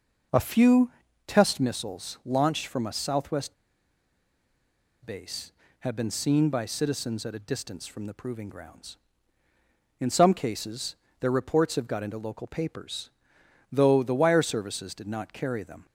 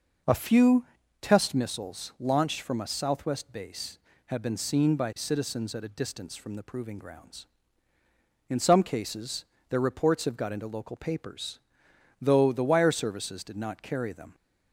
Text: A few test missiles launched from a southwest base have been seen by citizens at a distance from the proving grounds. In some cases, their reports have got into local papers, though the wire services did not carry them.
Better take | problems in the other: second | pauses between "few" and "test"; slight; at 0.9 s; 0.34 s long; slight in the second // pauses between "southwest" and "base"; strong; at 3.5 s; 1.5 s long

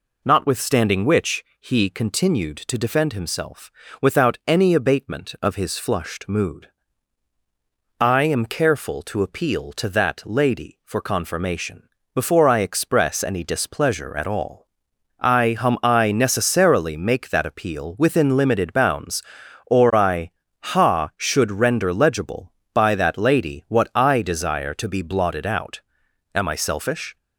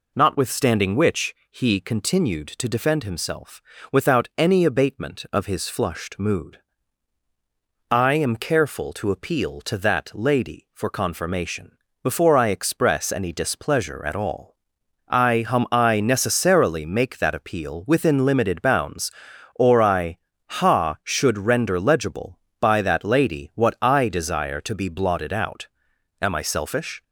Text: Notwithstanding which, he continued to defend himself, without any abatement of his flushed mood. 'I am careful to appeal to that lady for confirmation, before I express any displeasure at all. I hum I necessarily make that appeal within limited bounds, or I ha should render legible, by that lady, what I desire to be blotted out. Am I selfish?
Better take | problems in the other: neither | pauses between "I" and "ha"; slight; the same in both

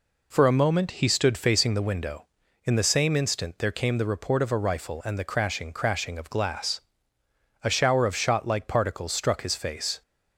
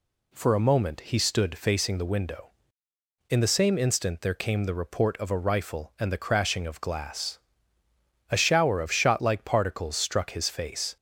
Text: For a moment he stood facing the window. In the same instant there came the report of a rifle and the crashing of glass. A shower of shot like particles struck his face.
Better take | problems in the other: second | says "crashing" twice; at 5.7 s

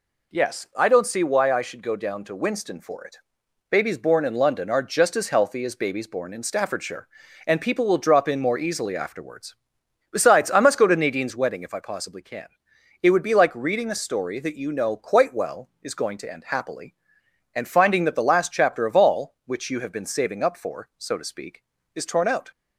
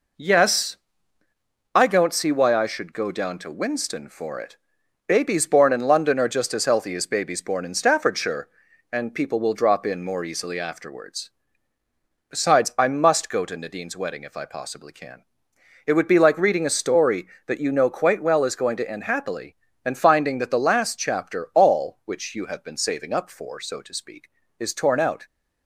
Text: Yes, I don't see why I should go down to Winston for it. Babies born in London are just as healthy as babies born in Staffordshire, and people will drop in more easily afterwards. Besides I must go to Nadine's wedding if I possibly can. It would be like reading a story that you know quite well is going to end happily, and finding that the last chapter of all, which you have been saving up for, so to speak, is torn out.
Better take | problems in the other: first | skips "of"; at 21.5 s

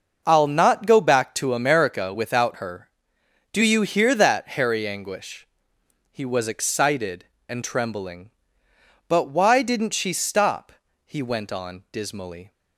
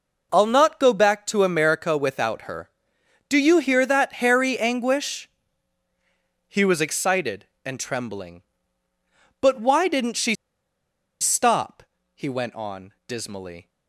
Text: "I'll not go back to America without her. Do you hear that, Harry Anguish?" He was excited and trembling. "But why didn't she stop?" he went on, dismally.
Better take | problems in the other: first | pauses between "she" and "stop"; noticeable; at 10.3 s; 0.85 s long

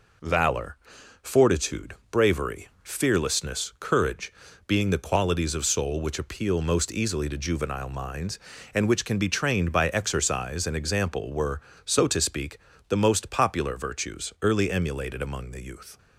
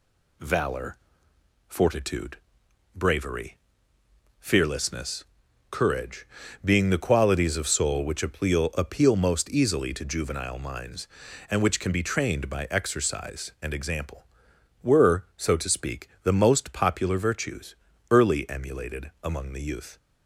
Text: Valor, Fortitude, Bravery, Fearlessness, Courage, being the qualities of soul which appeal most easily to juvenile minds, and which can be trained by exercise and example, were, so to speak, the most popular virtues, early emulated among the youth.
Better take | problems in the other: first | says "appeal" twice; at 8.7 s

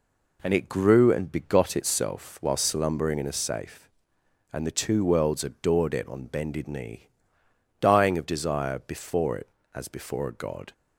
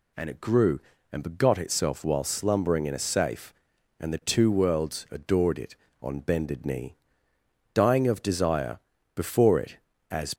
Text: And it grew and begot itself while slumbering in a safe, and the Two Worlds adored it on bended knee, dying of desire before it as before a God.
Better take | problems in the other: first | pauses between "desire" and "before"; slight; at 8.7 s; 0.34 s long // stops before "before a God"; at 10.3 s

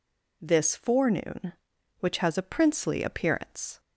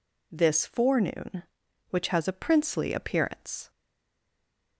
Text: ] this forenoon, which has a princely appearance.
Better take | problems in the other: first | stays silent after the last word; from 3.6 s on; 1.1 s long

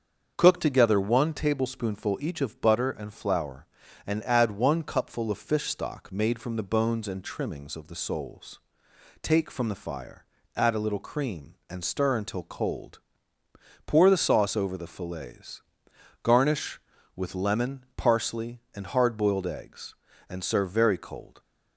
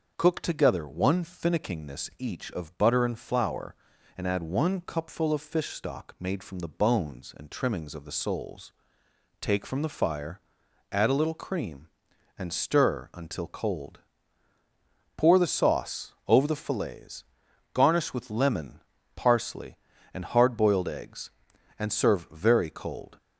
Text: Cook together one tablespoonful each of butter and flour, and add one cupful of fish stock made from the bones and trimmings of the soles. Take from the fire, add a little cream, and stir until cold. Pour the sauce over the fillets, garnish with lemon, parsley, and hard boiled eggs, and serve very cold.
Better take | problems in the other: first | starts louder than the rest; noticeable; until 1.1 s; 6 dB; also in the first // says "finickingness" for "tablespoonful"; at 1.2 s

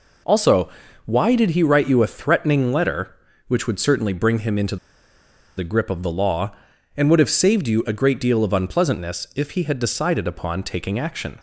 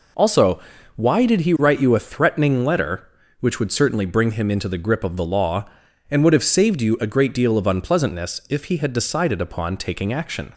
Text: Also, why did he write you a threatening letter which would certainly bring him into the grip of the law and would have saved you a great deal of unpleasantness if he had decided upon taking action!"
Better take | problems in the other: second | pauses between "into" and "the"; noticeable; at 4.7 s; 0.81 s long

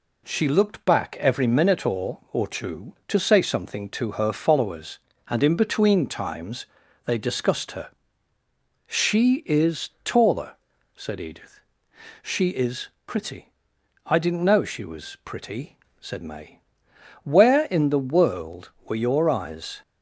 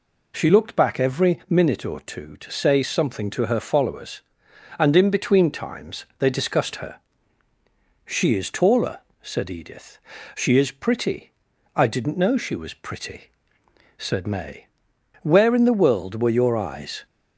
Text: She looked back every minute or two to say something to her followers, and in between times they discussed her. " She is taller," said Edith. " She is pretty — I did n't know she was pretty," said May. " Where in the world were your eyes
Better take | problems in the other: second | says "or" twice; at 2.3 s // pauses between "times" and "they"; at 6.6 s; 0.40 s long // pauses between "is" and "pretty"; slight; at 12.8 s; 0.16 s long

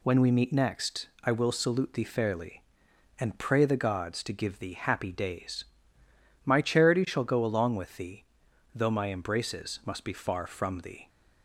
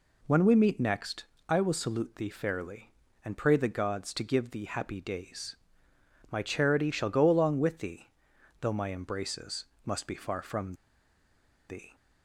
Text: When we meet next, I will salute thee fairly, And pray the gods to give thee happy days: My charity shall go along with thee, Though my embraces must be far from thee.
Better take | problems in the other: first | pauses between "embraces" and "must"; slight; at 9.6 s; 0.20 s long // pauses between "from" and "thee"; noticeable; at 10.7 s; 0.95 s long

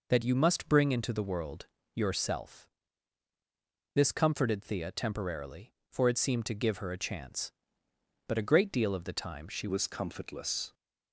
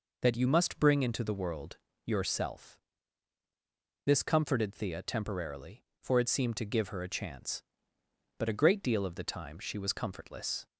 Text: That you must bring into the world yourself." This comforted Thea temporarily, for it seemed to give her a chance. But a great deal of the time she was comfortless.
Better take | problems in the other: second | pauses between "world" and "yourself"; slight; at 1.6 s; 0.30 s long; slight in the second // changes voice at "was"; from 9.6 s on; 1.1 s long

